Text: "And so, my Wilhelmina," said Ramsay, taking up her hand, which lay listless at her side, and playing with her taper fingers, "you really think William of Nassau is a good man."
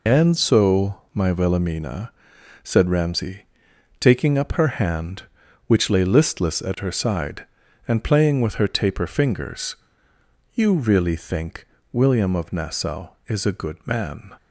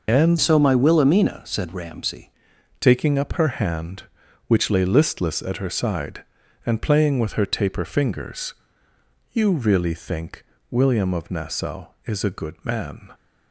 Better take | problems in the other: first | changes voice from "so" to "Ramsay"; from 0.4 to 2.3 s; 1.9 s long // pauses between "think" and "William"; slight; at 10.4 s; 0.26 s long; slight in the first

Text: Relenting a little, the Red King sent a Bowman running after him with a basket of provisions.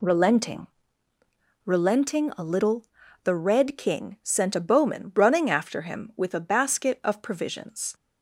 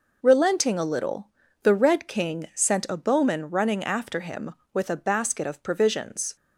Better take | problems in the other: second | says "Relenting" twice; at 1.6 s

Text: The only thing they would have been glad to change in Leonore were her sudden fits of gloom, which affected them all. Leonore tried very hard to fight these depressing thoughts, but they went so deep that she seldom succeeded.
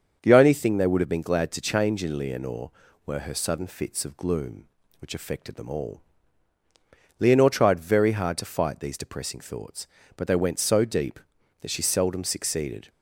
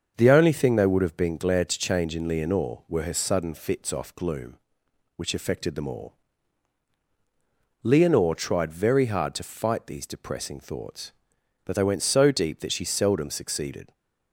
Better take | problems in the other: first | starts louder than the rest; until 1.1 s; 6.5 dB; also in the first // says "off" for "of"; at 3.9 s

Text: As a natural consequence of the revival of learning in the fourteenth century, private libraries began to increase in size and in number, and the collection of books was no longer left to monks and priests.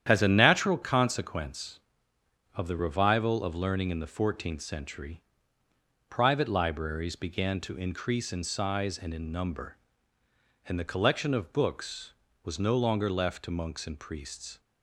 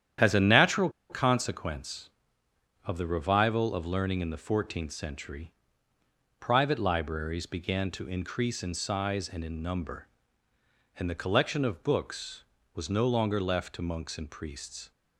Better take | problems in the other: first | starts louder than the rest; strong; until 1.4 s; 10 dB; strong in the first // pauses between "natural" and "consequence"; slight; at 0.8 s; 0.20 s long

